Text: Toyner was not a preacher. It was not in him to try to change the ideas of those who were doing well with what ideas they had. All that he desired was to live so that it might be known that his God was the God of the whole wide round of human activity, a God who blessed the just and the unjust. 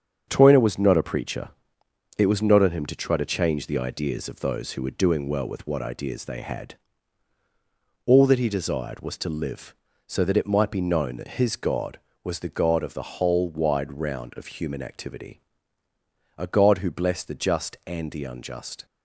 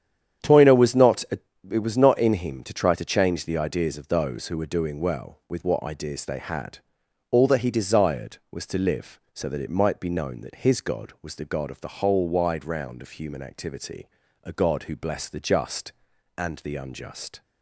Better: first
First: starts louder than the rest; until 1.2 s; 7 dB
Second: starts louder than the rest; strong; until 1.8 s; 9 dB // skips "preacher"; at 1.5 s

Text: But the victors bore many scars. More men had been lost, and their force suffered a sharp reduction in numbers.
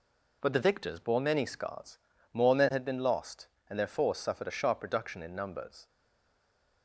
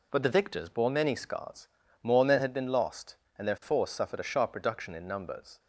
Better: second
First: stays silent after the last word; from 5.8 s on; 1.0 s long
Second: none

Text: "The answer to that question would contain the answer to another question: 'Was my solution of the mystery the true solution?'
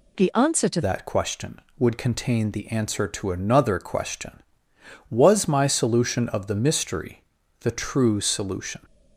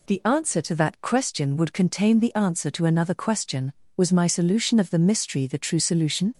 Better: second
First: changes voice at "that"; from 0.8 s on; 8.0 s long // pauses between "mystery" and "the"; at 7.2 s; 0.38 s long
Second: none

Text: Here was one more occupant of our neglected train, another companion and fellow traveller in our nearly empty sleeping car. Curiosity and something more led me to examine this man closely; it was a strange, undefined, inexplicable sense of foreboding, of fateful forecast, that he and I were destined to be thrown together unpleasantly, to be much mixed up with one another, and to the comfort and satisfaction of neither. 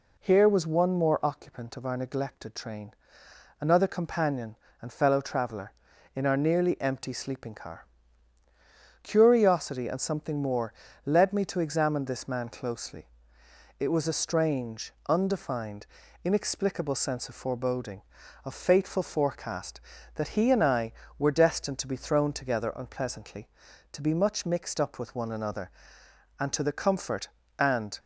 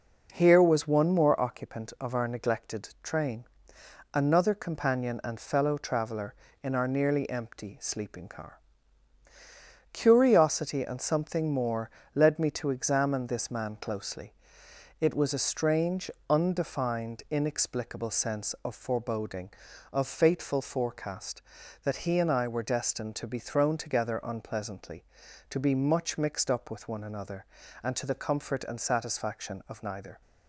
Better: second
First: pauses between "more" and "led"; slight; at 10.7 s; 0.32 s long // stops before "satisfaction of neither"; at 27.9 s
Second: pauses between "more" and "led"; slight; at 11.9 s; 0.24 s long

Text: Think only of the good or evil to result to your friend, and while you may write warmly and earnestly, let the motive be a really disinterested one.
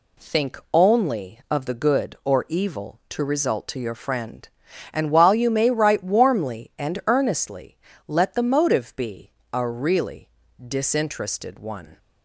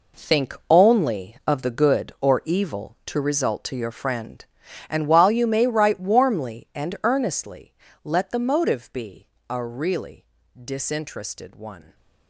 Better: first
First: pauses between "be" and "a"; slight; at 9.3 s; 0.22 s long // pauses between "really" and "disinterested"; at 10.2 s; 0.38 s long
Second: gets quieter; strong; throughout; 11 dB // pauses between "be" and "a"; slight; at 9.2 s; 0.22 s long // pauses between "really" and "disinterested"; at 10.2 s; 0.38 s long

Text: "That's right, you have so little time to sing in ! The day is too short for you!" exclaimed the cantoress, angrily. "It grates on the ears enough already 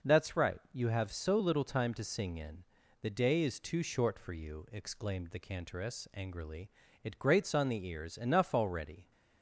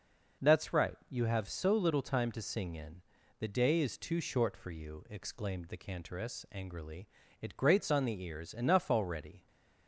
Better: neither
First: none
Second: none

